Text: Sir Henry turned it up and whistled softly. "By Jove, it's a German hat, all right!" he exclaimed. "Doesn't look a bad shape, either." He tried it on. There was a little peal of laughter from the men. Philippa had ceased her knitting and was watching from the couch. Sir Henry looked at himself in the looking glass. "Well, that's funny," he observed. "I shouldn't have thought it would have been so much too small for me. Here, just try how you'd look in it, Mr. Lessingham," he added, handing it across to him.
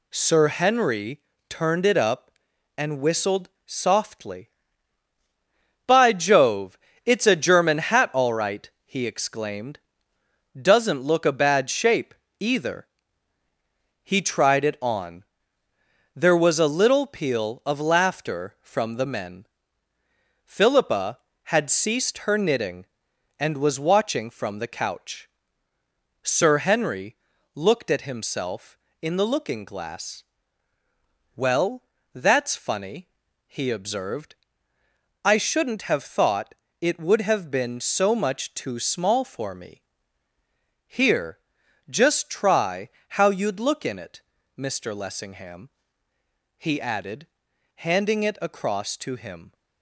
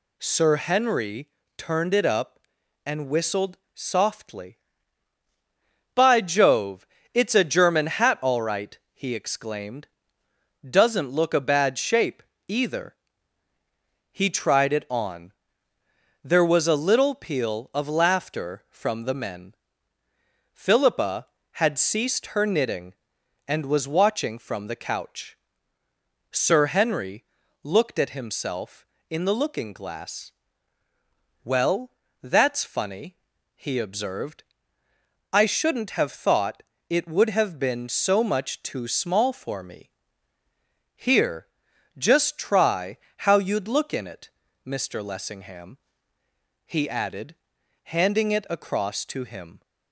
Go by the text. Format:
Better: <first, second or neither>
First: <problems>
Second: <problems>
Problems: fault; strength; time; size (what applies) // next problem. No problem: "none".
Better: second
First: gets quieter; noticeable; throughout; 6 dB // pauses between "Henry" and "turned"; slight; at 1.1 s; 0.30 s long // pauses between "whistled" and "softly"; slight; at 3.4 s; 0.16 s long // pauses between "Henry" and "looked"; at 27.1 s; 0.38 s long // pauses between "thought" and "it"; slight; at 36.5 s; 0.26 s long // pauses between "try" and "how"; slight; at 42.8 s; 0.20 s long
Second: pauses between "Henry" and "turned"; slight; at 1.2 s; 0.30 s long // pauses between "whistled" and "softly"; slight; at 3.5 s; 0.16 s long // pauses between "Henry" and "looked"; at 27.2 s; 0.38 s long // pauses between "thought" and "it"; slight; at 36.6 s; 0.26 s long // pauses between "try" and "how"; slight; at 42.9 s; 0.20 s long